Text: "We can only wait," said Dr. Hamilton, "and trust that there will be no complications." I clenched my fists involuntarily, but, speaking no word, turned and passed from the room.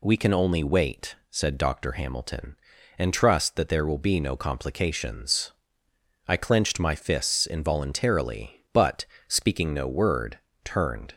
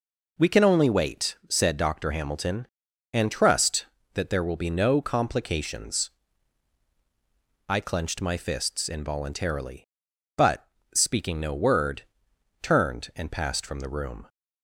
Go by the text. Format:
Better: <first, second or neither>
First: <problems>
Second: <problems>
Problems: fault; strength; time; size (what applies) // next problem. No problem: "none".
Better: second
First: stops before "and passed from the room"; at 11.1 s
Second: none